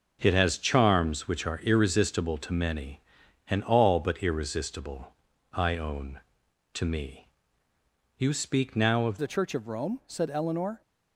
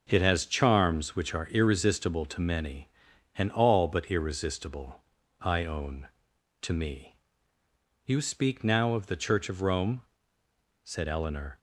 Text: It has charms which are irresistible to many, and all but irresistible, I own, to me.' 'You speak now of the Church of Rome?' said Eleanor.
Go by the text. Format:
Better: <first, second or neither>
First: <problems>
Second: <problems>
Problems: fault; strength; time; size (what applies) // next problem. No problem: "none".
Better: second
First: changes voice at "the"; from 9.1 s on; 1.7 s long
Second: none